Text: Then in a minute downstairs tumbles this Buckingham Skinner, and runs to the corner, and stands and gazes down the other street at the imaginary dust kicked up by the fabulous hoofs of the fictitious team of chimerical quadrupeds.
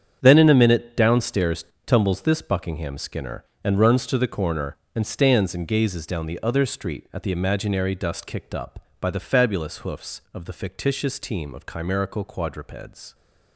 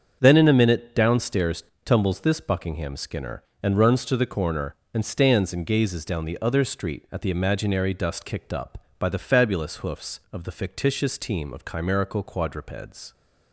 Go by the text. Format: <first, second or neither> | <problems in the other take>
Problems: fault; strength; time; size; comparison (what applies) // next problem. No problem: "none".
second | gets quieter; strong; throughout; 12 dB // starts louder than the rest; strong; until 1.2 s; 8 dB; strong in the second // pauses between "downstairs" and "tumbles"; slight; at 1.6 s; 0.22 s long; slight in the second